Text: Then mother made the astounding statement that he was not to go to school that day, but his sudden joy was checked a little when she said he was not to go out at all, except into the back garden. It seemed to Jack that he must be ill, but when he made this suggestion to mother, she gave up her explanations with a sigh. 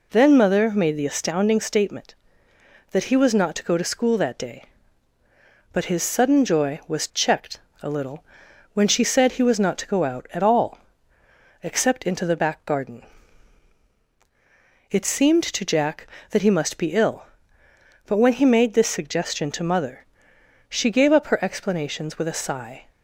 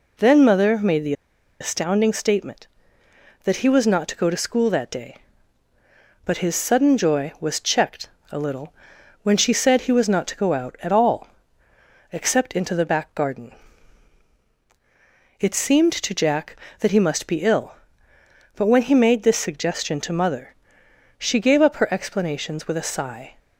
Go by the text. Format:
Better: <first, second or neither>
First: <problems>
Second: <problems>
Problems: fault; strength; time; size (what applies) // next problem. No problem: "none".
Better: first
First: pauses between "checked" and "a"; slight; at 7.6 s; 0.20 s long // pauses between "little" and "when"; noticeable; at 8.2 s; 0.48 s long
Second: pauses between "the" and "astounding"; noticeable; at 1.1 s; 0.47 s long // pauses between "checked" and "a"; slight; at 8.1 s; 0.20 s long // pauses between "little" and "when"; noticeable; at 8.7 s; 0.48 s long